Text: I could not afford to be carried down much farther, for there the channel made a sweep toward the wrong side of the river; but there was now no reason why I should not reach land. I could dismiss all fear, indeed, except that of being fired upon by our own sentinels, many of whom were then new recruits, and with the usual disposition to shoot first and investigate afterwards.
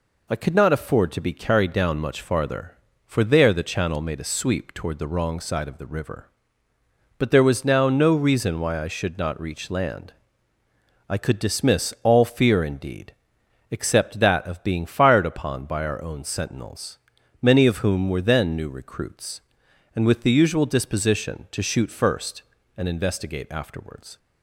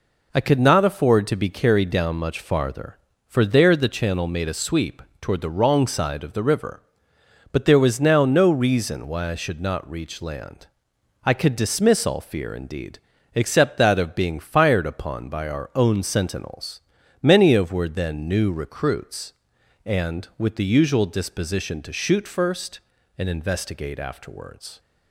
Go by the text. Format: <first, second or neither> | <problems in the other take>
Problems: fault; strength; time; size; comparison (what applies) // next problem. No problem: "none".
first | pauses between "sweep" and "toward"; slight; at 5.0 s; 0.20 s long // skips "whom"; at 17.7 s